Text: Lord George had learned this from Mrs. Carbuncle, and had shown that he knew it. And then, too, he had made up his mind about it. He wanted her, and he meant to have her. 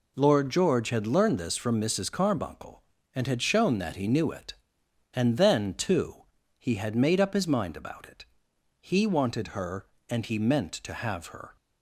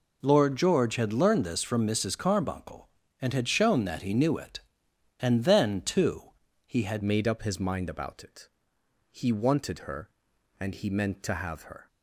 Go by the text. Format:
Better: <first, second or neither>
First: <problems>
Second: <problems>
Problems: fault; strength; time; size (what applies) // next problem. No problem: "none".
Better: first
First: none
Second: changes voice at "made"; from 7.0 s on; 4.8 s long